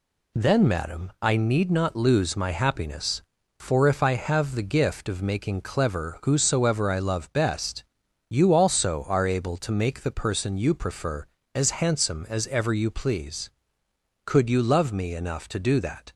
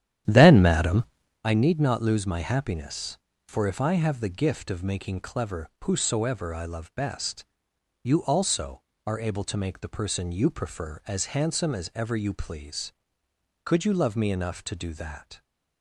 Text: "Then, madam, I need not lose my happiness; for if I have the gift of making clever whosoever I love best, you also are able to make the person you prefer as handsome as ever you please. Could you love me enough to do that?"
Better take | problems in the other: first | starts louder than the rest; strong; until 1.4 s; 11 dB // pauses between "clever" and "whosoever"; slight; at 5.6 s; 0.16 s long

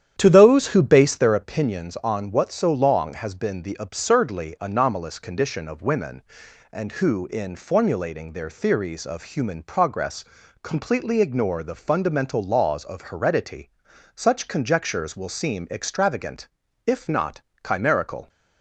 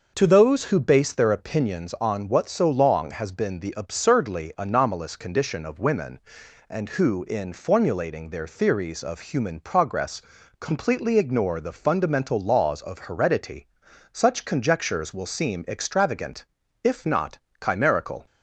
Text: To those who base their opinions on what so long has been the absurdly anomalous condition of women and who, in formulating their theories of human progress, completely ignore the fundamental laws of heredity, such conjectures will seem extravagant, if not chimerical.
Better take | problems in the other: second | starts louder than the rest; strong; until 1.4 s; 9.5 dB // pauses between "not" and "chimerical"; slight; at 17.4 s; 0.24 s long; slight in the second

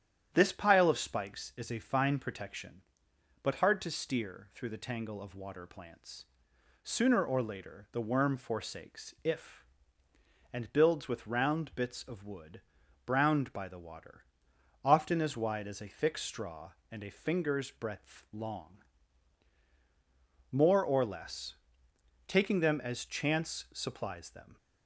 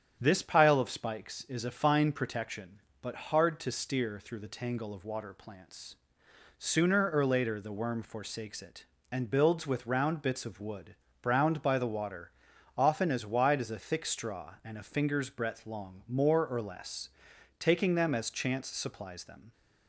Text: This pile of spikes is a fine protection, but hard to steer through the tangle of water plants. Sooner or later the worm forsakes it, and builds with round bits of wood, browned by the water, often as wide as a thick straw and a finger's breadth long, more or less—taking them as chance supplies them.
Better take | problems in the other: second | starts louder than the rest; strong; until 1.3 s; 10 dB; strong in the second // says "if" for "it"; at 9.2 s

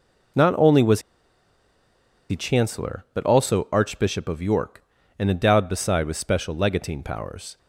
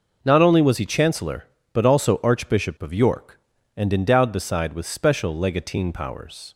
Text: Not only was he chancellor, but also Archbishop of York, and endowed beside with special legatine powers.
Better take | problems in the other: second | pauses between "was" and "he"; strong; at 1.0 s; 1.2 s long

